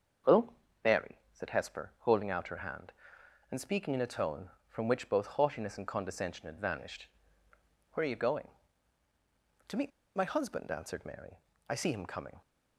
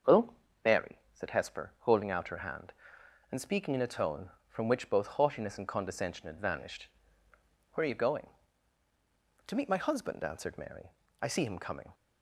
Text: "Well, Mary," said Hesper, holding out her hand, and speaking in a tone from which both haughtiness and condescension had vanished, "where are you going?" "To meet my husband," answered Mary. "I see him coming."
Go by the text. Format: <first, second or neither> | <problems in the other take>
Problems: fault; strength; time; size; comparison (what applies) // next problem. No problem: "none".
second | starts louder than the rest; until 1.7 s; 6.5 dB; also in the second // pauses between "meet" and "my"; slight; at 9.9 s; 0.26 s long